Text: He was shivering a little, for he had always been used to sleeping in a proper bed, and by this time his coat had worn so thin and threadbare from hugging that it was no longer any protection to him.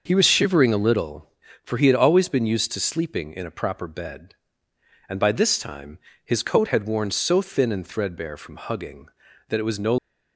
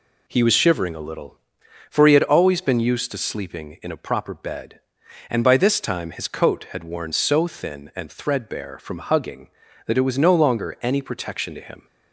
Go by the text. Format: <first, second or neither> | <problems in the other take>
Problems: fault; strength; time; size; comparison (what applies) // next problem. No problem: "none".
second | starts louder than the rest; until 1.0 s; 6 dB // pauses between "time" and "his"; slight; at 5.9 s; 0.26 s long // stops before "longer any protection to him"; at 9.9 s